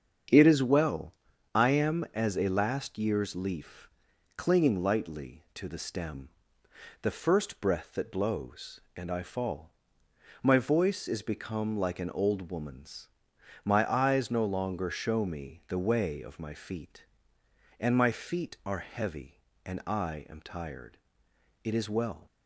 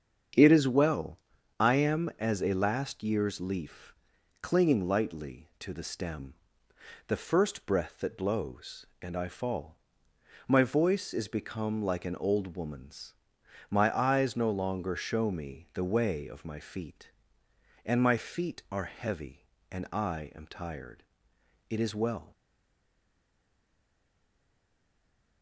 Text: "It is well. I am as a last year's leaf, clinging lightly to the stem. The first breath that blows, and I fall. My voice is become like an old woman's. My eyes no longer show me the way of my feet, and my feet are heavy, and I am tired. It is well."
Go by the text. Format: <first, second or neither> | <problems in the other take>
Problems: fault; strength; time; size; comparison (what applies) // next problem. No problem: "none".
first | starts louder than the rest; strong; until 1.7 s; 7.5 dB; strong in the first // stays silent after the last word; strong; from 22.3 s on; 3.1 s long